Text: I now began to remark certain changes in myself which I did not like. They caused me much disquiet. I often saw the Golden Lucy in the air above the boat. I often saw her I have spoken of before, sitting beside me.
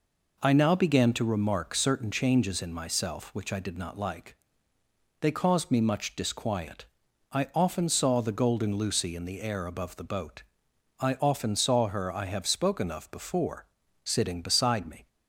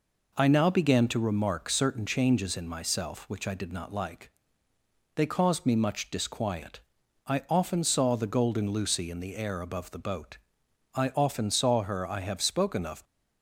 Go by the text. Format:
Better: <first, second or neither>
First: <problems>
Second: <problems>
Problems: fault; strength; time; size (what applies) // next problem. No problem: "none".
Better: first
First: none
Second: stops before "before sitting beside me"; at 13.0 s